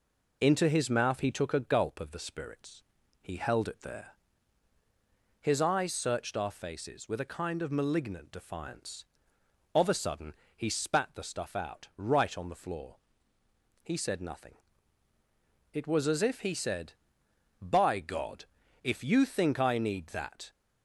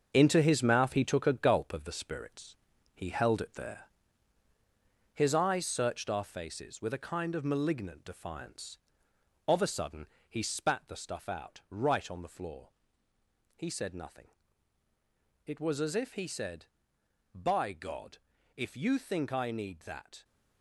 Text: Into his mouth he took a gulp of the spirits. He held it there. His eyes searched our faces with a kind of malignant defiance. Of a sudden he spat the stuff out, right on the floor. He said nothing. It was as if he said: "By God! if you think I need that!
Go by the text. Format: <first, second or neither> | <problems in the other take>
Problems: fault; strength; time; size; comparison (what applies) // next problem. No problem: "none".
first | gets quieter; throughout; 7 dB // pauses between "sudden" and "he"; slight; at 10.0 s; 0.22 s long; slight in the first